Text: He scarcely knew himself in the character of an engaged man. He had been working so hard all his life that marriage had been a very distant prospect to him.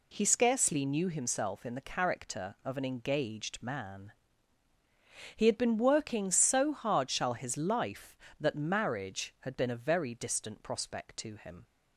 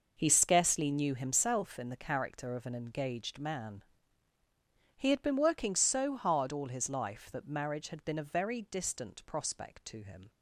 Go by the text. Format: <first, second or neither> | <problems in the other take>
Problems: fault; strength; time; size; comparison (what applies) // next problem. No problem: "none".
second | says "shall" for "all"; at 7.0 s